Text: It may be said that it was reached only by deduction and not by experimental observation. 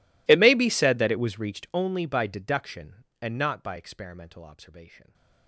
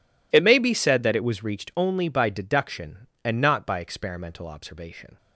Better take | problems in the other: second | gets quieter; strong; throughout; 30.5 dB

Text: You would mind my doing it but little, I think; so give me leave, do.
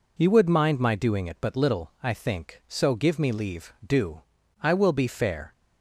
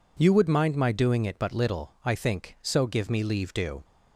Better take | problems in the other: second | goes on to say "I will be fair"; noticeable; from 4.6 s on; 0.90 s long

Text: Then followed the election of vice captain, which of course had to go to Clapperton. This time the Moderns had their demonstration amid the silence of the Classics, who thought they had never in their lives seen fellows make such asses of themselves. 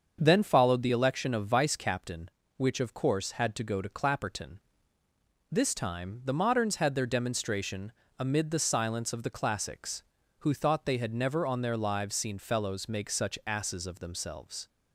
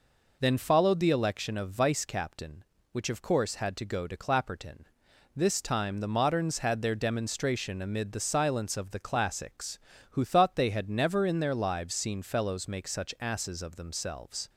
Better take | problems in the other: second | starts louder than the rest; until 1.2 s; 7 dB // pauses between "demonstration" and "amid"; slight; at 7.9 s; 0.26 s long // says "on" for "in"; at 11.4 s

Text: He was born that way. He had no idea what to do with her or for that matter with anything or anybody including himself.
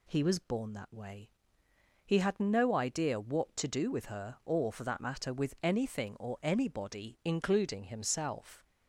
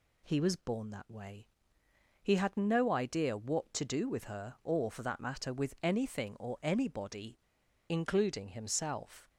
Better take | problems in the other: first | pauses between "anybody" and "including"; noticeable; at 7.3 s; 0.52 s long

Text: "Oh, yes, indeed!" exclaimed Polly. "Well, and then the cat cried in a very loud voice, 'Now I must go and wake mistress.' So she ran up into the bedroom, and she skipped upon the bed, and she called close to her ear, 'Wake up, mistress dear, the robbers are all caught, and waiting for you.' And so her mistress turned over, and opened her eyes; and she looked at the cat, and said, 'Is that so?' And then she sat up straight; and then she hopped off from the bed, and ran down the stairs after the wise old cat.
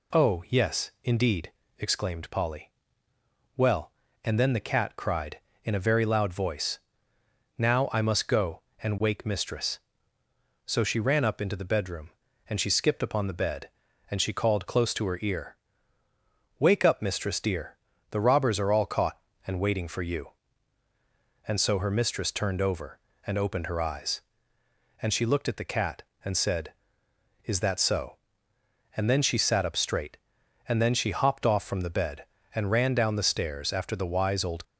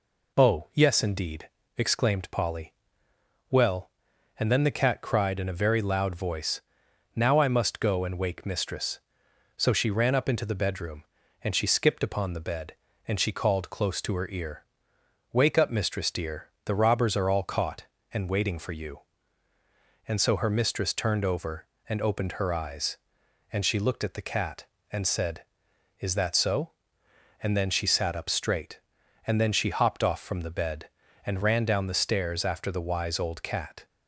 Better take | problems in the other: second | stops before "cat"; at 34.6 s

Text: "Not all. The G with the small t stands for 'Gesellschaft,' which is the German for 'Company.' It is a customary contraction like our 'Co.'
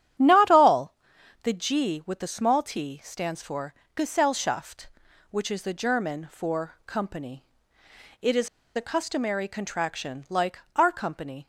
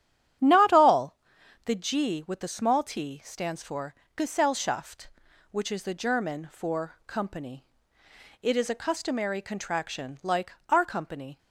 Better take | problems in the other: second | starts louder than the rest; strong; until 1.6 s; 10 dB; strong in the second // pauses between "for" and "Gesellschaft"; slight; at 3.7 s; 0.20 s long; slight in the second // pauses between "is" and "a"; slight; at 8.4 s; 0.27 s long // pauses between "like" and "our"; slight; at 10.5 s; 0.18 s long; slight in the second

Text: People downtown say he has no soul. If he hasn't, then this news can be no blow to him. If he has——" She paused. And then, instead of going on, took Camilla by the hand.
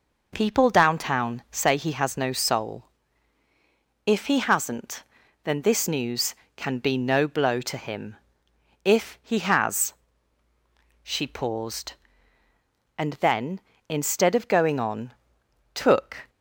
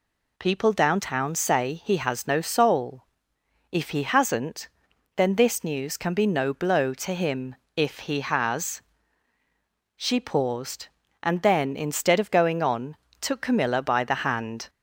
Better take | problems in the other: second | stops before "Camilla by the hand"; at 16.2 s

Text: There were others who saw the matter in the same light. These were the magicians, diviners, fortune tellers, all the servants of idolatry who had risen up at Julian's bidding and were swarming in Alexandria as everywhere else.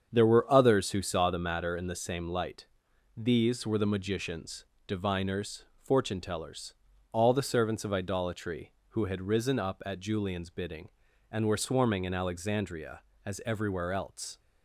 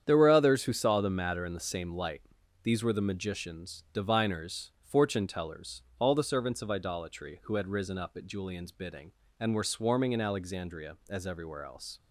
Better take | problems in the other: neither | starts louder than the rest; strong; the same in both

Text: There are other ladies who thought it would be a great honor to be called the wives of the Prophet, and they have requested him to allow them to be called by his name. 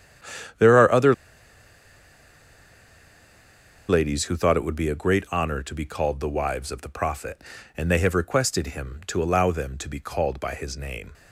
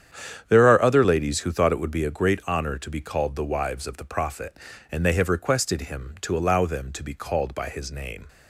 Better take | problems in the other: second | starts louder than the rest; strong; until 4.3 s; 9 dB; strong in the second // pauses between "other" and "ladies"; strong; at 1.1 s; 2.7 s long

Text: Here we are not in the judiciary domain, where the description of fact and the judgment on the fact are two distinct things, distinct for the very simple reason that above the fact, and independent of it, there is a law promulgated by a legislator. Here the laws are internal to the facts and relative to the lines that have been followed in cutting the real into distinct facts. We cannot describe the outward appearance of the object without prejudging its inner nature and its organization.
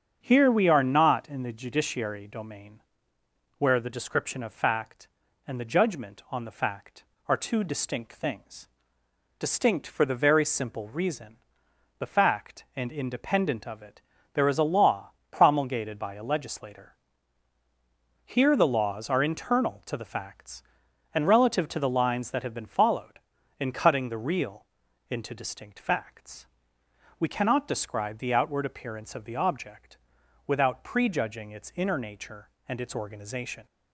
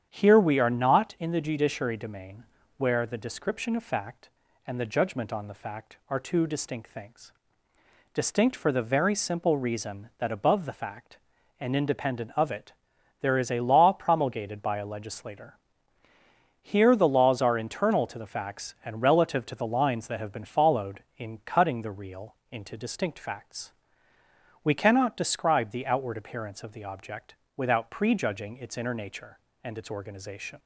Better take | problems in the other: second | starts louder than the rest; until 1.2 s; 7 dB; strong in the second // skips "that above"; at 11.6 s // pauses between "law" and "promulgated"; slight; at 15.1 s; 0.20 s long // pauses between "real" and "into"; at 24.6 s; 0.44 s long; slight in the second // pauses between "object" and "without"; noticeable; at 29.9 s; 0.50 s long; slight in the second

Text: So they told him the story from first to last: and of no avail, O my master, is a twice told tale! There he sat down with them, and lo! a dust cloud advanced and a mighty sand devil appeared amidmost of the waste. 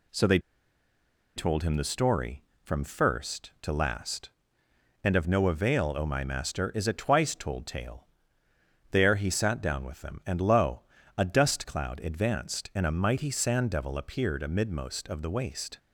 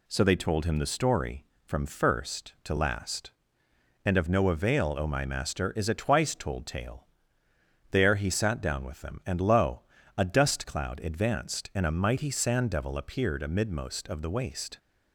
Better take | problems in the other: second | pauses between "they" and "told"; noticeable; at 0.3 s; 0.97 s long

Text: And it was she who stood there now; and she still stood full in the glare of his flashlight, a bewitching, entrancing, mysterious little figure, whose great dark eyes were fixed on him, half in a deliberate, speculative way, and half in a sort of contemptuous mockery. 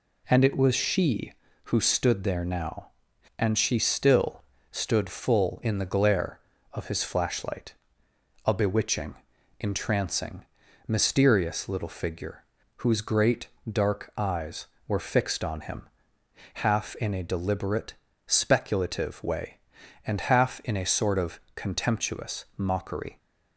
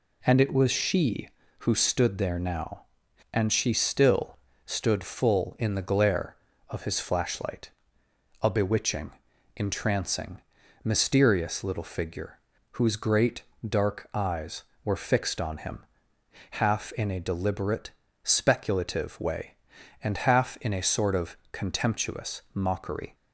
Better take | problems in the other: neither | pauses between "still" and "stood"; slight; the same in both // pauses between "great" and "dark"; slight; the same in both // pauses between "of" and "contemptuous"; slight; the same in both

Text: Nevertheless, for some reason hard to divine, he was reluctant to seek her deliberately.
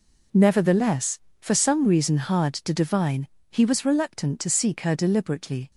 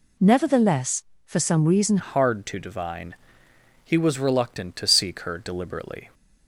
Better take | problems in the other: first | changes voice at "hard"; from 1.9 s on; 4.2 s long

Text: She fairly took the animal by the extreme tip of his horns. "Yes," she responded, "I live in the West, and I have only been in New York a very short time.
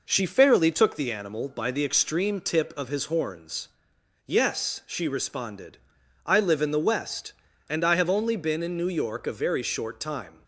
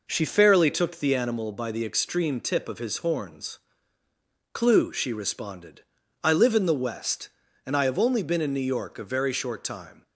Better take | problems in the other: first | says "Clue" for "Yes"; at 4.5 s

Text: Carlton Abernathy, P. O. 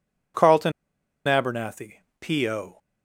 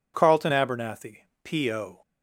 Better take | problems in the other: second | pauses between "Carlton" and "Abernathy"; noticeable; at 0.7 s; 0.55 s long

